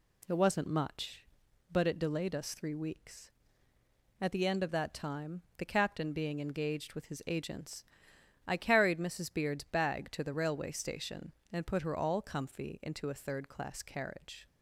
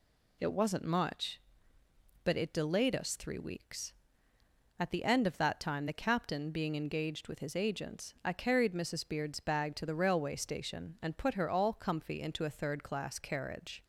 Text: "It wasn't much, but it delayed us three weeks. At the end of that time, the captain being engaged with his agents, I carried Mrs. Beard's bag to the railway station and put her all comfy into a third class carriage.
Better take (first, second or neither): first